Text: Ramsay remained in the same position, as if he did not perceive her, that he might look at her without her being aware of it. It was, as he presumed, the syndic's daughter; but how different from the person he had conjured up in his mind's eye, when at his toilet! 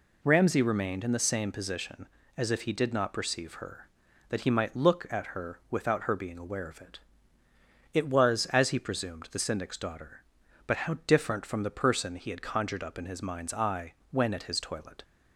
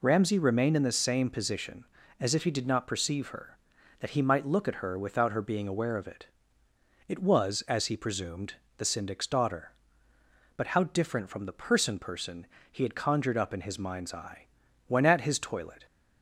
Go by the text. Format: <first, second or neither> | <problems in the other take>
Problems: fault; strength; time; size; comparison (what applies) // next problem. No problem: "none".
first | says "person" twice; at 11.9 s